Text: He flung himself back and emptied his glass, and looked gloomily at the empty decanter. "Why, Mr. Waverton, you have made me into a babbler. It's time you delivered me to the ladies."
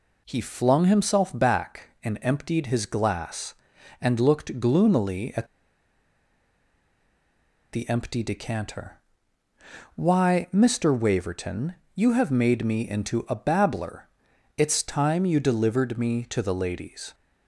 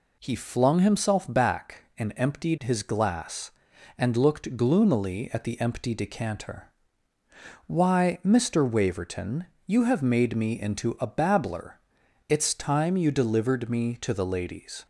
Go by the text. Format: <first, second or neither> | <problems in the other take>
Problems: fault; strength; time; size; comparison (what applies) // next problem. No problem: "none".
second | pauses between "at" and "the"; strong; at 5.4 s; 2.2 s long